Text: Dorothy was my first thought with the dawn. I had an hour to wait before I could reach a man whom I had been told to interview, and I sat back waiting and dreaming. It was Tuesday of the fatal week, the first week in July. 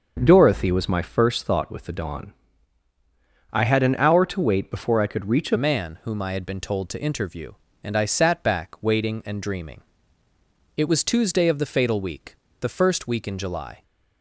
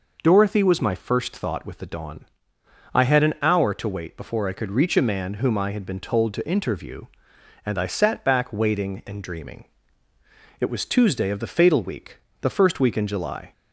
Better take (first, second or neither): second